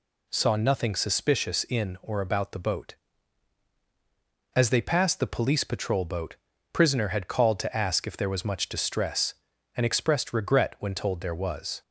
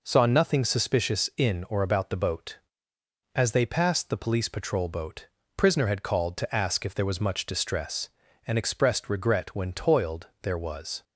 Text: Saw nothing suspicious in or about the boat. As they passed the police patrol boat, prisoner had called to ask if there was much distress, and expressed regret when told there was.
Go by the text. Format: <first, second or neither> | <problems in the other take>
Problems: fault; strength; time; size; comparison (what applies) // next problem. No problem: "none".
first | says "toiled" for "told"; at 9.7 s